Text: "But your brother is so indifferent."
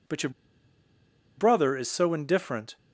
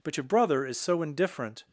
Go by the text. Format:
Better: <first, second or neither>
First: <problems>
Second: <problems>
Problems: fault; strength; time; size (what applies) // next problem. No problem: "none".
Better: second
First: pauses between "your" and "brother"; at 0.2 s; 1.0 s long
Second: none